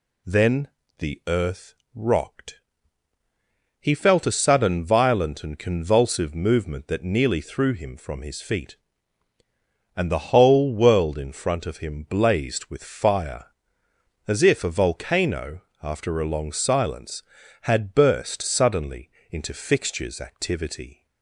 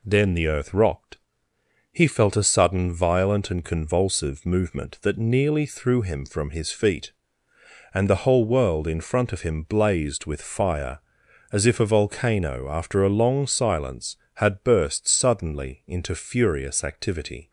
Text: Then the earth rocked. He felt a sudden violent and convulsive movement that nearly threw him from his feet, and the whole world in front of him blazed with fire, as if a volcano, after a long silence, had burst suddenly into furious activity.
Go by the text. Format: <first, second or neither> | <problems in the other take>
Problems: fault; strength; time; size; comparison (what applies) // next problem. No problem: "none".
second | pauses between "Then" and "the"; slight; at 0.6 s; 0.30 s long // pauses between "earth" and "rocked"; slight; at 1.7 s; 0.20 s long // pauses between "suddenly" and "into"; slight; at 19.0 s; 0.20 s long // says "fixtures" for "furious"; at 19.5 s